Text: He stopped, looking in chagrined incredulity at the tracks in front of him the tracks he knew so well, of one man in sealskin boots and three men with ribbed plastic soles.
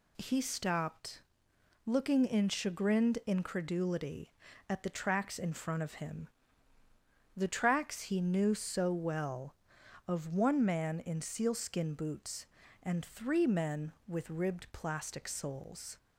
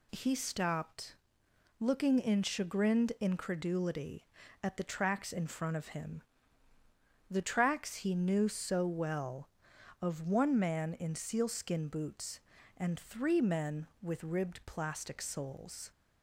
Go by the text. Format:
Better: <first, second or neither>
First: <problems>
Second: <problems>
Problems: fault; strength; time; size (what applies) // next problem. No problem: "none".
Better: neither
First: pauses between "him" and "the"; at 6.2 s; 1.1 s long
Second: pauses between "him" and "the"; at 6.2 s; 1.1 s long